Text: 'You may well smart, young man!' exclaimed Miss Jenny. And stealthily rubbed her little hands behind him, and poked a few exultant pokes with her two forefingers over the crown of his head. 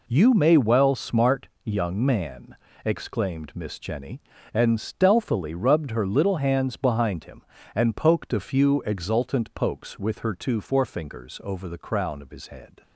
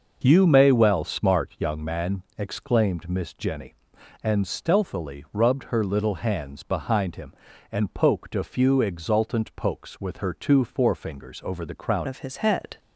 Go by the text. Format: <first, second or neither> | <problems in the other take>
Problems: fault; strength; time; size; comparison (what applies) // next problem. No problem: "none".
first | changes voice at "of"; from 12.0 s on; 0.7 s long